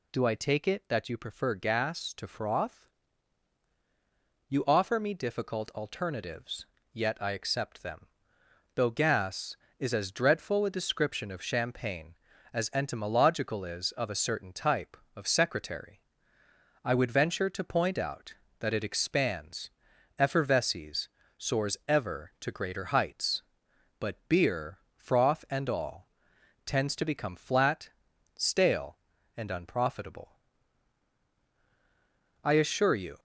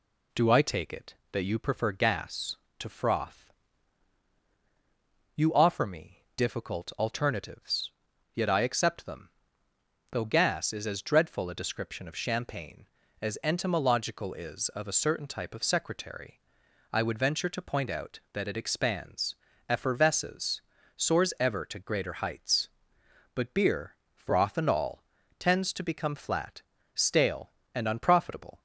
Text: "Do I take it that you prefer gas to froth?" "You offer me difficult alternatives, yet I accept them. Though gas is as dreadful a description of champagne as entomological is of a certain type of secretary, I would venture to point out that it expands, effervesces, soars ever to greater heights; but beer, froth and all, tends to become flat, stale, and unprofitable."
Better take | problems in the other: second | goes on to say "I assure you"; noticeable; from 32.4 s on; 0.76 s long

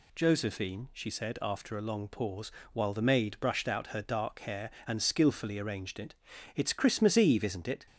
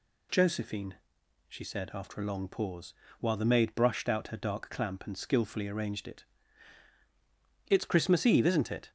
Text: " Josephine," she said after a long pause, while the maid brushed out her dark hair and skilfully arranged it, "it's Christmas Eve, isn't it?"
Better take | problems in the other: first | says "clamp" for "hair"; at 4.7 s

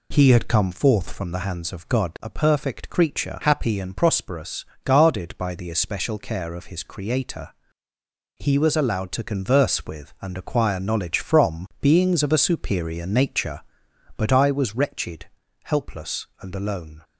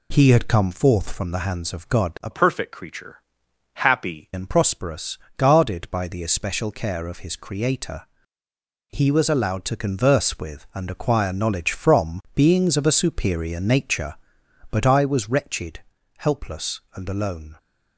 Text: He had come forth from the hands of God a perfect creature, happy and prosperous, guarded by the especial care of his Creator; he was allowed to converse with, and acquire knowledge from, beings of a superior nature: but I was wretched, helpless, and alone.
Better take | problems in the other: first | changes voice from "perfect" to "happy"; from 2.3 to 4.2 s; 1.9 s long

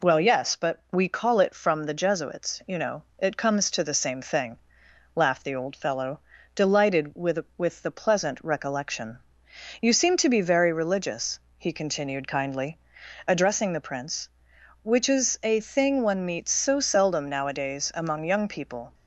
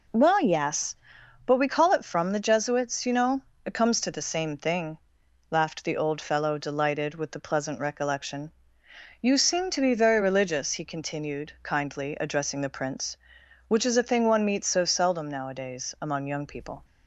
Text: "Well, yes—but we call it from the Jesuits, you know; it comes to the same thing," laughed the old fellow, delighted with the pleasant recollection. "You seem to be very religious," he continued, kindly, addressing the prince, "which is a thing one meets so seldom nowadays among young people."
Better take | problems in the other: second | says "with" twice; at 7.5 s

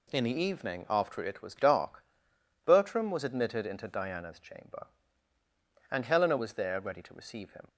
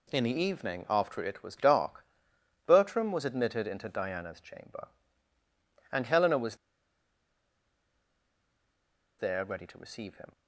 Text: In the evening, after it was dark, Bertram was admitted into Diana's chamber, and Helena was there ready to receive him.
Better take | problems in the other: first | pauses between "was" and "there"; strong; at 6.5 s; 2.6 s long

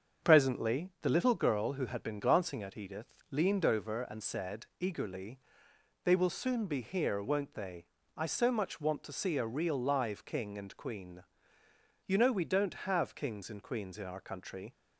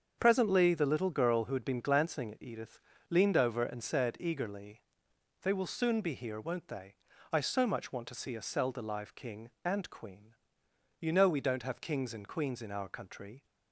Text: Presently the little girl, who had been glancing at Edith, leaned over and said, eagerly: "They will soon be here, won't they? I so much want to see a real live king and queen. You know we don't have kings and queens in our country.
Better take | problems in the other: first | starts louder than the rest; until 1.2 s; 7 dB; strong in the first // says "selda" for "real"; at 8.4 s

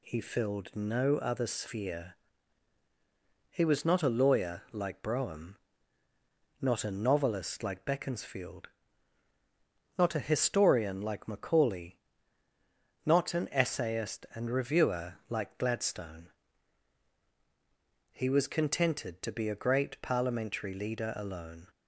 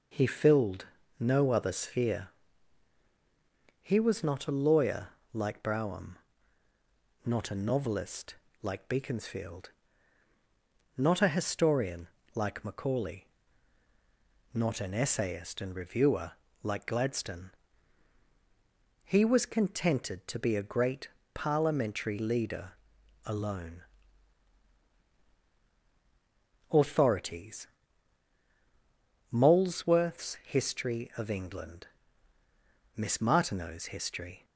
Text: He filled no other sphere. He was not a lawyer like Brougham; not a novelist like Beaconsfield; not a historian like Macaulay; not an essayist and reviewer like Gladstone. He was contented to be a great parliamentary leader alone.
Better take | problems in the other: first | pauses between "filled" and "no"; slight; at 0.8 s; 0.34 s long // pauses between "lawyer" and "like"; slight; at 5.0 s; 0.24 s long // pauses between "novelist" and "like"; slight; at 8.3 s; 0.26 s long // pauses between "historian" and "like"; slight; at 12.0 s; 0.26 s long // pauses between "reviewer" and "like"; slight; at 16.3 s; 0.30 s long; slight in the first // pauses between "great" and "parliamentary"; slight; at 21.0 s; 0.24 s long // pauses between "leader" and "alone"; noticeable; at 22.7 s; 0.52 s long // goes on to say "AUTHORITIES Molesworth's History of England Miss Martineau's History"; strong; from 26.7 s on; 7.7 s long

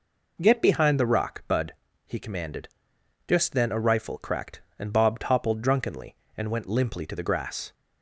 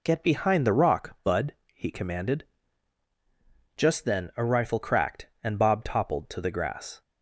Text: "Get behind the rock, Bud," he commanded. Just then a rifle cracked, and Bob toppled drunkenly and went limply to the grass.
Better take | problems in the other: first | skips "drunkenly and went limply"; at 6.2 s

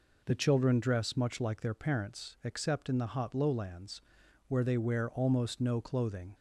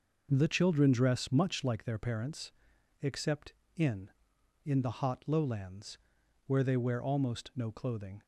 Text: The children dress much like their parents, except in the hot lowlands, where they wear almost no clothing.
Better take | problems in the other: first | says "in" twice; at 4.6 s

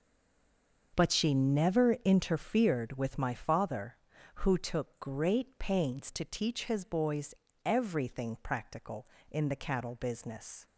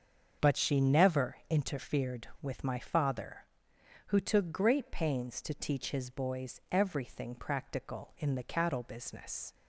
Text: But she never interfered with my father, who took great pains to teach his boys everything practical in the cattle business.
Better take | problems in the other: second | stays silent before the first word; slight; until 0.9 s; 0.9 s long // starts louder than the rest; until 2.0 s; 6 dB; also in the second // pauses between "boys" and "everything"; slight; at 7.3 s; 0.30 s long

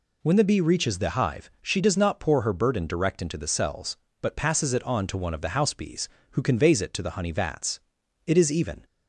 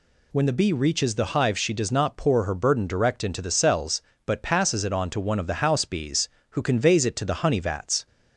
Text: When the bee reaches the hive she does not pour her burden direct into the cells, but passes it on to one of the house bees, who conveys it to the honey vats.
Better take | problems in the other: second | goes on to say "It is even"; from 8.2 s on; 0.58 s long

